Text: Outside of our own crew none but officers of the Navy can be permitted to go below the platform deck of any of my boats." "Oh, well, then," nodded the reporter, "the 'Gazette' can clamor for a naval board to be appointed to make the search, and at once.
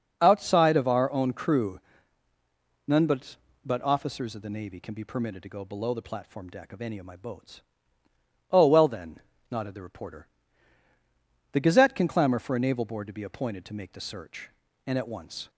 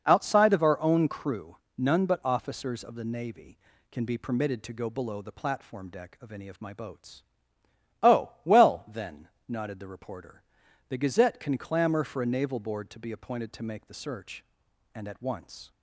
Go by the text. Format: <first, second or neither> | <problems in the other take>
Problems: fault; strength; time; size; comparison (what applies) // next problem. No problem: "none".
second | starts louder than the rest; noticeable; until 1.2 s; 6 dB // pauses between "crew" and "none"; at 1.7 s; 1.0 s long; slight in the second // says "but" twice; at 3.6 s